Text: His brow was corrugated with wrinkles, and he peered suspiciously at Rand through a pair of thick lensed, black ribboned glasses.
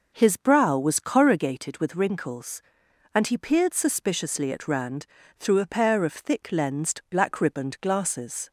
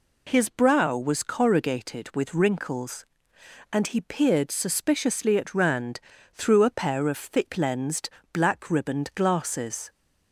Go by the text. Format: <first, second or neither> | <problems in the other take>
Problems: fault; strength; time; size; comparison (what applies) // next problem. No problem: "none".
neither | pauses between "Rand" and "through"; slight; the same in both